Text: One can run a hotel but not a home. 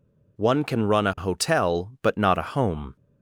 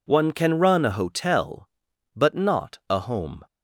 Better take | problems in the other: neither | none

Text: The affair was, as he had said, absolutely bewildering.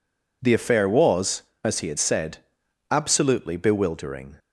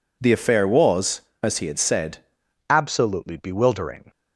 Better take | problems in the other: first | changes voice at "absolutely"; from 2.6 s on; 1.5 s long

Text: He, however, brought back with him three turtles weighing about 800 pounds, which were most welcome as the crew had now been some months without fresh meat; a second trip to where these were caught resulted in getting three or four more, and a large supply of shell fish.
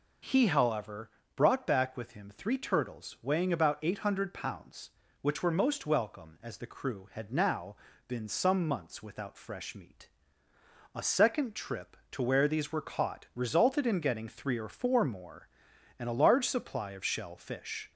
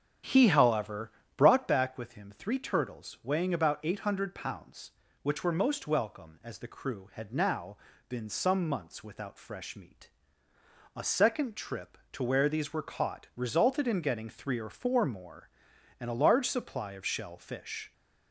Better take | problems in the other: first | starts louder than the rest; strong; until 1.8 s; 9 dB // pauses between "now" and "been"; slight; at 7.7 s; 0.32 s long; slight in the first

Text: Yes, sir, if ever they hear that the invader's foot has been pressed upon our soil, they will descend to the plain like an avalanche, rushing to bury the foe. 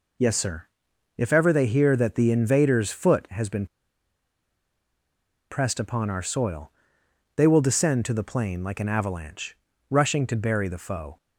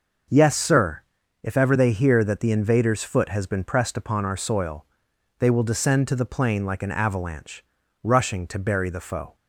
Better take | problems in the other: second | pauses between "been" and "pressed"; strong; at 3.6 s; 1.8 s long

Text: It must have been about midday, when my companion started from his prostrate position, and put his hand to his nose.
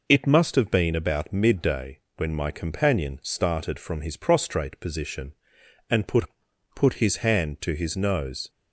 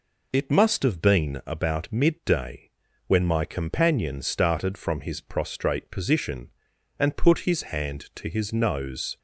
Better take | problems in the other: second | says "put" twice; at 6.7 s

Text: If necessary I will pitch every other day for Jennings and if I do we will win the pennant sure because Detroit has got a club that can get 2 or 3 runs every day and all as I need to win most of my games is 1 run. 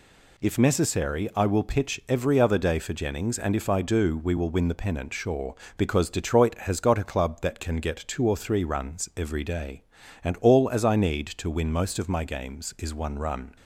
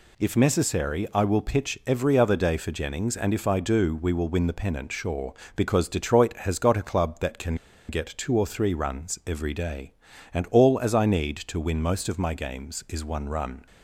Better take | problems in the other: first | pauses between "can" and "get"; slight; at 7.5 s; 0.33 s long

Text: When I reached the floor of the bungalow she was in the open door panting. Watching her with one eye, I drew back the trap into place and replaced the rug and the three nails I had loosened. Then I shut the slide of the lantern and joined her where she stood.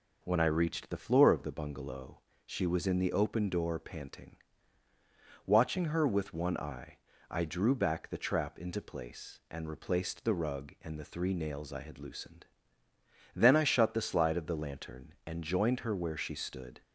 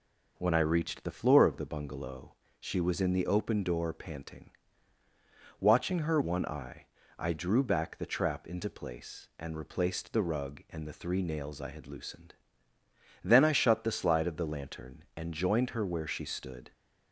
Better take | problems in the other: first | pauses between "bungalow" and "she"; slight; at 2.3 s; 0.24 s long; slight in the first // skips "with"; at 6.2 s

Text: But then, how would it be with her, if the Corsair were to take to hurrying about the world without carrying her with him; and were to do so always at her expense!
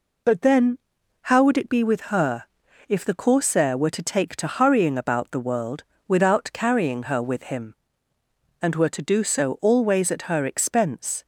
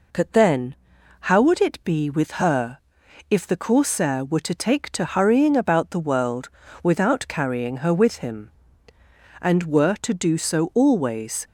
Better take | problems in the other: first | pauses between "world" and "without"; slight; at 6.4 s; 0.34 s long; slight in the first // stops before "at her expense"; at 11.4 s

